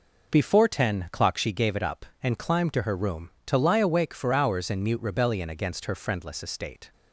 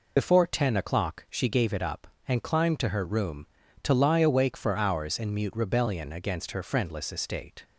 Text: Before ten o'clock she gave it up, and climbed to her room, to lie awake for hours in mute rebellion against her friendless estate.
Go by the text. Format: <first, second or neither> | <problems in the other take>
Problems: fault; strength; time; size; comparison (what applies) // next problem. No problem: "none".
first | loses the start of "Before"; at 0.1 s; 50 ms